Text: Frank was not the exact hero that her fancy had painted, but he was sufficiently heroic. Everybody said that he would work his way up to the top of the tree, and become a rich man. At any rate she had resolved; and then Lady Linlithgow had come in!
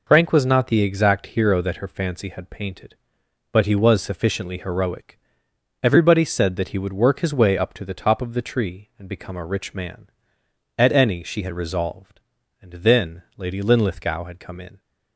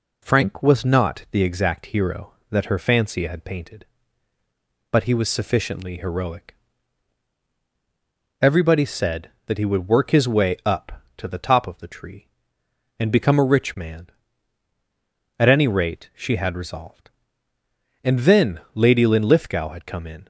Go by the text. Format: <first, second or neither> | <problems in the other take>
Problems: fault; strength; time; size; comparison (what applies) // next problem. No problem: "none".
second | skips "rate"; at 11.2 s